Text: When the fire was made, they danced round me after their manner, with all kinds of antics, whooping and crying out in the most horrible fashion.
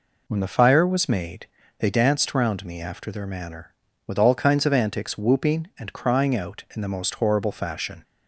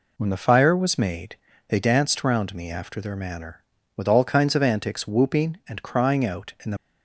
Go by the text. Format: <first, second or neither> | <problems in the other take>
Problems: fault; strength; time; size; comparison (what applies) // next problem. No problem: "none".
first | stops before "most horrible fashion"; at 6.7 s